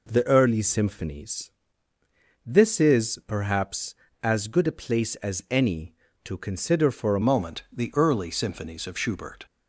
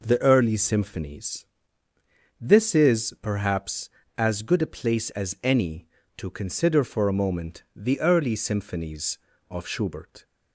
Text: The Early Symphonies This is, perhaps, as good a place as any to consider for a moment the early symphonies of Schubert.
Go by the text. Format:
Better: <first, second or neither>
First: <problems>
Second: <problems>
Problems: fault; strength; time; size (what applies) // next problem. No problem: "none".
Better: second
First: pauses between "Symphonies" and "This"; noticeable; at 1.5 s; 0.94 s long // changes voice at "moment"; from 7.2 s on; 2.2 s long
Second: pauses between "Symphonies" and "This"; noticeable; at 1.4 s; 0.94 s long